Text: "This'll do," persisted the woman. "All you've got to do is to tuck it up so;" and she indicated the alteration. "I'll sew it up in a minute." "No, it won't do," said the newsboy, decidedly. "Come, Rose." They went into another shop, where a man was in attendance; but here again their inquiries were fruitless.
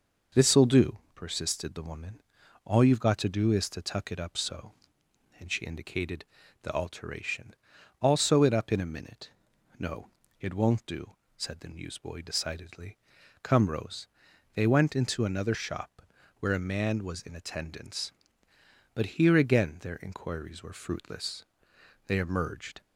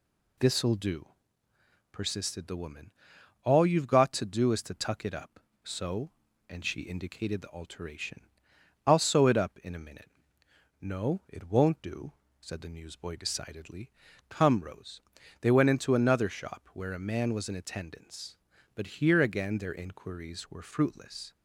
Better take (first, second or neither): second